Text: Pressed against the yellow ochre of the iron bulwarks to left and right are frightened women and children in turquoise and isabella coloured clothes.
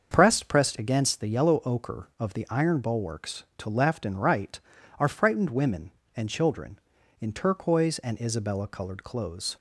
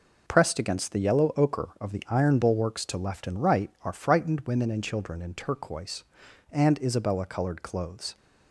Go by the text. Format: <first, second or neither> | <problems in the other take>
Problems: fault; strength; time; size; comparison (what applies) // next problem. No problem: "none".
second | starts louder than the rest; until 1.1 s; 6.5 dB // says "Pressed" twice; at 0.4 s